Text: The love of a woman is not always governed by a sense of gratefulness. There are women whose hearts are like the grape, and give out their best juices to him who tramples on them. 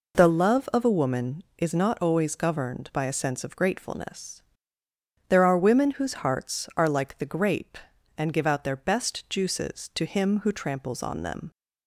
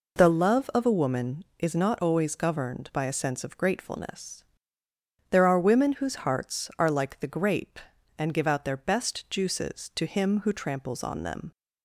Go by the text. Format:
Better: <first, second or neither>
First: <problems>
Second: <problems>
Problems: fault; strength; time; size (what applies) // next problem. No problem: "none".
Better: neither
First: none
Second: none